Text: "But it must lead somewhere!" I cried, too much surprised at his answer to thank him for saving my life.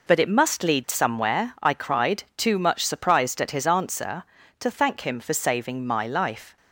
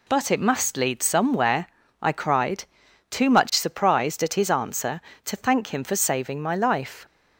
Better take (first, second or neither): neither